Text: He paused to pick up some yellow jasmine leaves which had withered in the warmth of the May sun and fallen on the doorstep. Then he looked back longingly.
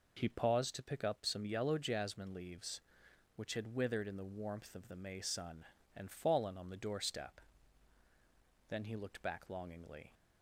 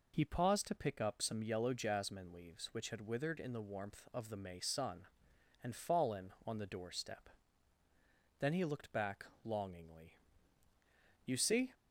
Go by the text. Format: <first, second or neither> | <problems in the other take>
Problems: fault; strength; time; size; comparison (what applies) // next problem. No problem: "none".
first | pauses between "back" and "longingly"; slight; at 9.2 s; 0.18 s long // goes on to say "You see"; slight; from 11.2 s on; 0.48 s long